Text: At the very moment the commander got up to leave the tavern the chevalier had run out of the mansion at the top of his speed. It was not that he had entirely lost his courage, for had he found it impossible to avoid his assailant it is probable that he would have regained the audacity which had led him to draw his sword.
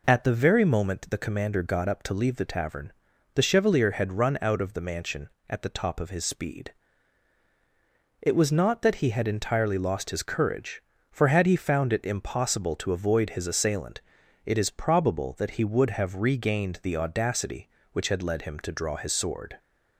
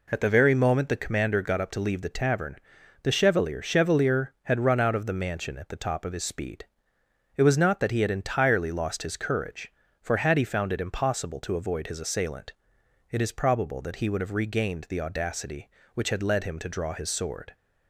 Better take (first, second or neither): first